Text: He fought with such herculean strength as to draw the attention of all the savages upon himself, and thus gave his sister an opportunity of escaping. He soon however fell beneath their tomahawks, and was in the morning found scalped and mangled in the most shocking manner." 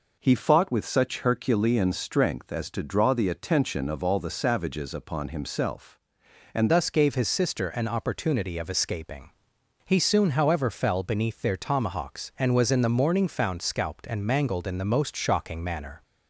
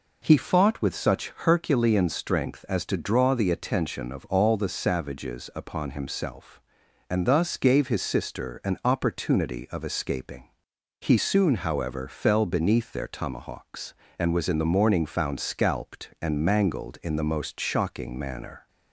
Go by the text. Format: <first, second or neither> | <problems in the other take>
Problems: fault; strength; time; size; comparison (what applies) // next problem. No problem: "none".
second | changes voice at "thus"; from 6.6 s on; 9.4 s long